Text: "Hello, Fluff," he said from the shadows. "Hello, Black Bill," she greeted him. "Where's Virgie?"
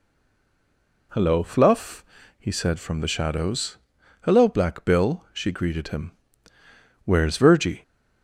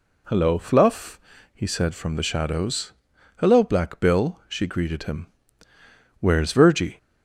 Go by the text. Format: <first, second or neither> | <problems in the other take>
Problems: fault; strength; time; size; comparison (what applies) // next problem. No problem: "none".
second | stays silent before the first word; until 1.1 s; 1.1 s long